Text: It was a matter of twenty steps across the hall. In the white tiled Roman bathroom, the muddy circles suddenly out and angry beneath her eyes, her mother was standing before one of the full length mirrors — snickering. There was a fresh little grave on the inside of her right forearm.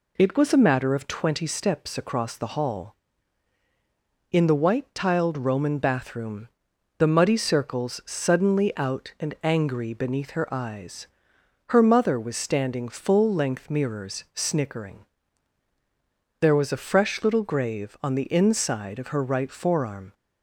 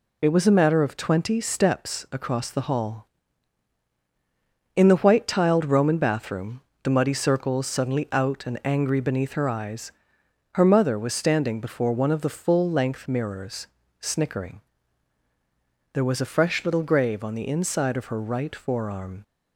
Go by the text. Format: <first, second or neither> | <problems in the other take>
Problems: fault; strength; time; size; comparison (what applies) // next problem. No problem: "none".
second | skips "before one of the"; at 12.8 s